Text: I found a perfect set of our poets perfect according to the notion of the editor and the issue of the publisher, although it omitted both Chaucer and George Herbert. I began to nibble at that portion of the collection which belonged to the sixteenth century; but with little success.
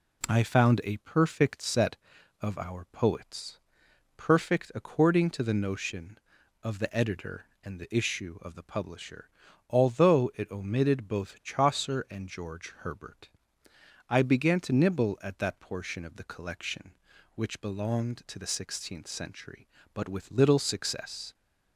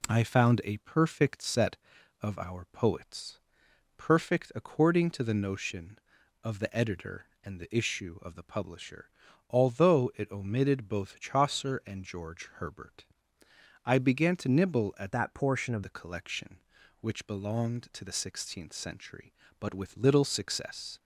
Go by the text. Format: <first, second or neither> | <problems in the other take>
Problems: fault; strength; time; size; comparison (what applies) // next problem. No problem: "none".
first | pauses between "poets" and "perfect"; noticeable; at 3.3 s; 0.58 s long; noticeable in the first // changes voice from "that" to "of"; from 15.1 to 15.8 s; 0.7 s long